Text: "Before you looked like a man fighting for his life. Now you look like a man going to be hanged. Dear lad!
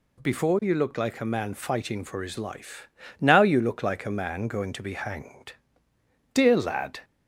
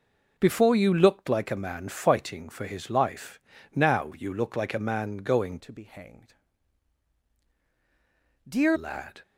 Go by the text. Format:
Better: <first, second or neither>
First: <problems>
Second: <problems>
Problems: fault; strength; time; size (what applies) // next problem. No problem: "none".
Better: first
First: none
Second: changes voice from "to" to "Dear"; from 5.5 to 8.7 s; 3.2 s long